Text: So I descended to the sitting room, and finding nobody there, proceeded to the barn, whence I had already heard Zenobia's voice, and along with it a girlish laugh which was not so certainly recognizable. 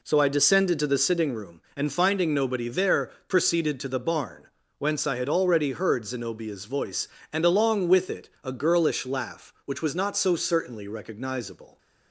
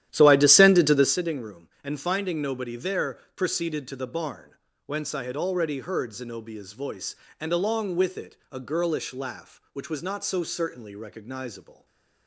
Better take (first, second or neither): first